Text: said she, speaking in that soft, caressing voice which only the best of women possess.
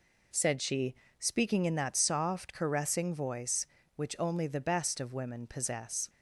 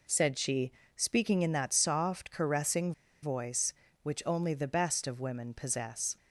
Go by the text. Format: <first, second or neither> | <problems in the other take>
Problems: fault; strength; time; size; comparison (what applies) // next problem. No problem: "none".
first | pauses between "caressing" and "voice"; slight; at 2.9 s; 0.31 s long